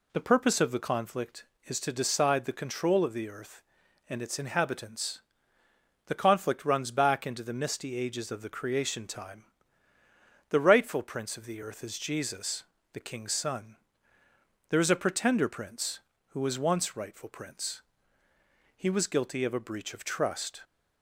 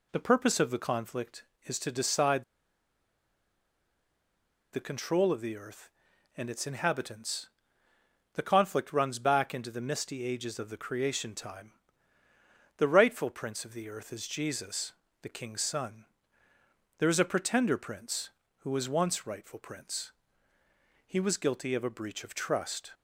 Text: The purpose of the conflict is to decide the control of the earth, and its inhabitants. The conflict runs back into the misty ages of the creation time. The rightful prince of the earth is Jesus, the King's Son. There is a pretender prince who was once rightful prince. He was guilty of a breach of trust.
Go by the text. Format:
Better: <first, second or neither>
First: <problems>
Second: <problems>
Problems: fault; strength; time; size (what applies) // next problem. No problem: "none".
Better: first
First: none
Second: pauses between "decide" and "the"; strong; at 2.4 s; 2.2 s long